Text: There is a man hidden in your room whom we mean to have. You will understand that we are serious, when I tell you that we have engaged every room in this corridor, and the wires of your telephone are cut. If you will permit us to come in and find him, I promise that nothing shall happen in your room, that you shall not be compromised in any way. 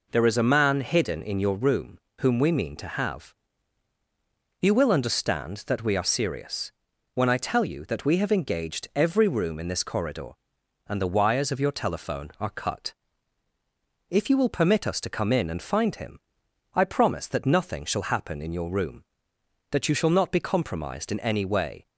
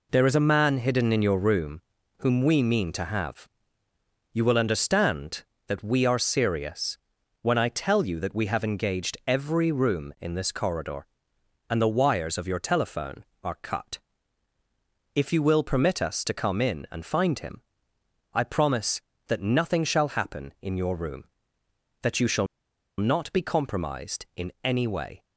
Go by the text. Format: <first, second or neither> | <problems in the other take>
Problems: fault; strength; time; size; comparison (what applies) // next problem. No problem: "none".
first | pauses between "room" and "whom"; slight; at 1.8 s; 0.34 s long; slight in the first // pauses between "shall" and "not"; noticeable; at 22.4 s; 0.53 s long